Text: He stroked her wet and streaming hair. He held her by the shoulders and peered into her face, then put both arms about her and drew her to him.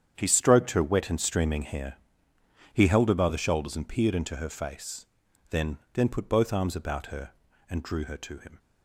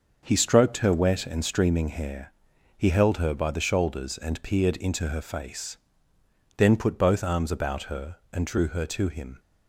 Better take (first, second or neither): second